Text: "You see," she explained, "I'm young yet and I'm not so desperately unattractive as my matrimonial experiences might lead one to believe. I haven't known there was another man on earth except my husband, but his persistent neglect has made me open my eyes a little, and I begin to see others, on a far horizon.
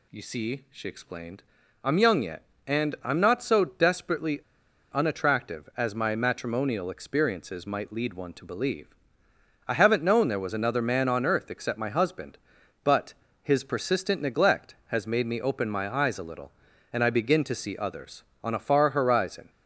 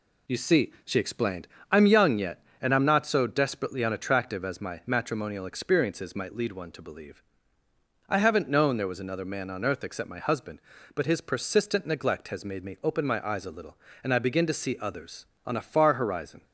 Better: second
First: pauses between "desperately" and "unattractive"; noticeable; at 4.4 s; 0.53 s long // pauses between "but" and "his"; slight; at 13.1 s; 0.30 s long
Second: none

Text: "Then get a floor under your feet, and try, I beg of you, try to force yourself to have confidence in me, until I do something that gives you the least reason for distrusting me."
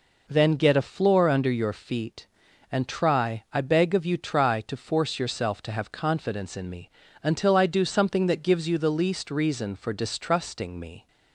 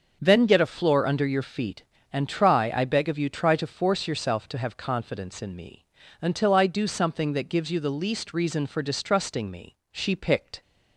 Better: first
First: none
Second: starts louder than the rest; until 1.2 s; 6.5 dB // goes on to say "She picked"; noticeable; from 9.9 s on; 0.68 s long

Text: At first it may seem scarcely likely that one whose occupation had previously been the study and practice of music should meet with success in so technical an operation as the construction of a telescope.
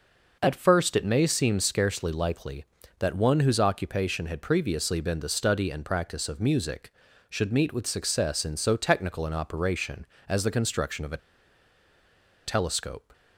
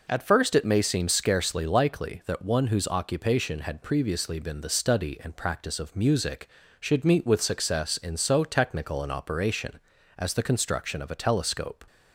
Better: second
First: pauses between "a" and "telescope"; strong; at 11.1 s; 1.2 s long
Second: none

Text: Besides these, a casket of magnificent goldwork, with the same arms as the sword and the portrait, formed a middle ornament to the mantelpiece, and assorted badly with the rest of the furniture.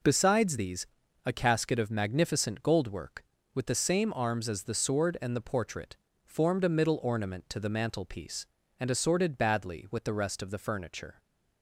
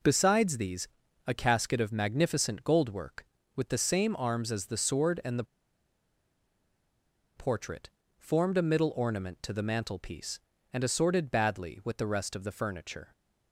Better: first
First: none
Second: pauses between "the" and "portrait"; strong; at 5.4 s; 1.9 s long

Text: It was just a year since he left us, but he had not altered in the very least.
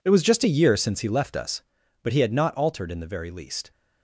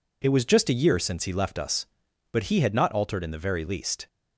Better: second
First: gets quieter; strong; throughout; 14.5 dB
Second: none

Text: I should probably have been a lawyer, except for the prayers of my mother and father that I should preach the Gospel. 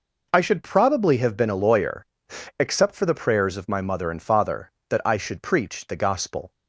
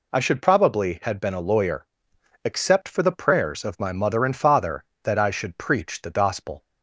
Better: first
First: none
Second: says "had" for "have"; at 1.0 s

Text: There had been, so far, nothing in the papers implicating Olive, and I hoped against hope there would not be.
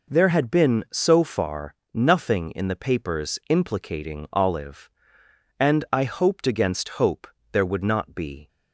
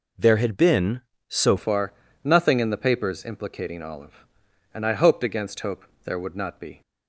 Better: first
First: pauses between "hope" and "there"; slight; at 7.2 s; 0.24 s long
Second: changes voice at "far"; from 1.5 s on; 5.3 s long // pauses between "hope" and "there"; slight; at 5.8 s; 0.20 s long

